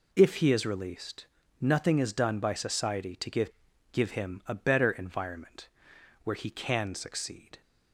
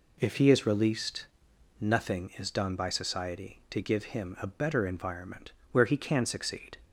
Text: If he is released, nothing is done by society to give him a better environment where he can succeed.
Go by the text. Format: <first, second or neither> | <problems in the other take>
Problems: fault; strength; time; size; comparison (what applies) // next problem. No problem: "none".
second | says "give" twice; at 3.9 s // pauses between "environment" and "where"; noticeable; at 5.6 s; 0.56 s long; slight in the second